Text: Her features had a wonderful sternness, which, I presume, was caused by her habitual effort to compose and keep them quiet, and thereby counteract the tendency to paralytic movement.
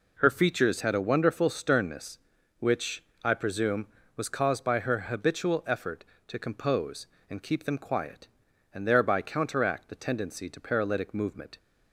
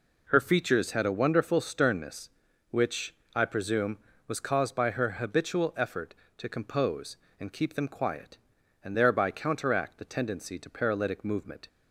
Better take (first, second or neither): neither